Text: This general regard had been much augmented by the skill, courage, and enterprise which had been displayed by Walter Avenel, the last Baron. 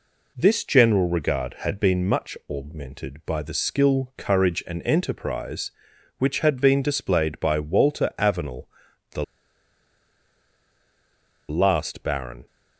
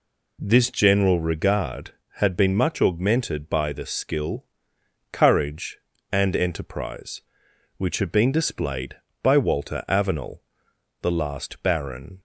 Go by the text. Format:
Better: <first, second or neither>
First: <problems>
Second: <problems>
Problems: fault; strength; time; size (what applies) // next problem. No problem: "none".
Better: second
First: pauses between "the" and "last"; strong; at 9.2 s; 2.2 s long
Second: none